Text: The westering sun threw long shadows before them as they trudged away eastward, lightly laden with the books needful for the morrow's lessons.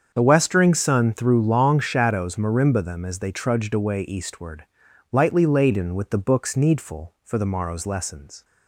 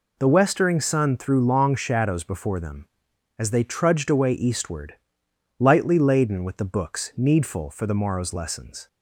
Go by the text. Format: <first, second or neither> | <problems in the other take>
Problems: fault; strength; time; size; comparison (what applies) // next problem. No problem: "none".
second | starts louder than the rest; strong; until 1.1 s; 7 dB // says "marimba" for "before"; at 2.3 s